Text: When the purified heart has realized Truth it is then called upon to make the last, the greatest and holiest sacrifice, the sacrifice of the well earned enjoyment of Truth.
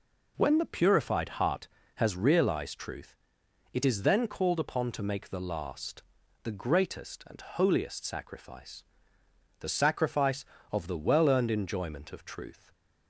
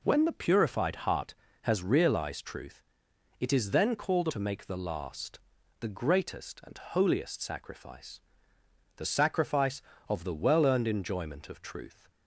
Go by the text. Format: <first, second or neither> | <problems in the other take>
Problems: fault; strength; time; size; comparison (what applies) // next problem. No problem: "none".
first | pauses between "Truth" and "it"; noticeable; at 2.8 s; 0.56 s long; noticeable in the first // skips "upon"; at 4.2 s